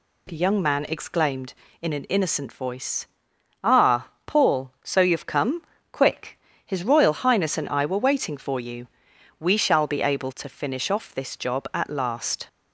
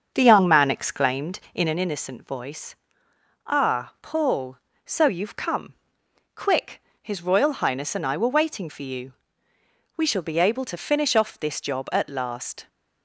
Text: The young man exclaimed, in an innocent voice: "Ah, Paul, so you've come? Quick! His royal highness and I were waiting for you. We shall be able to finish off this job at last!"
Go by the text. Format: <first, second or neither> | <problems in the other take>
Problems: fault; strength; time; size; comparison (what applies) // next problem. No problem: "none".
first | starts louder than the rest; until 1.8 s; 7 dB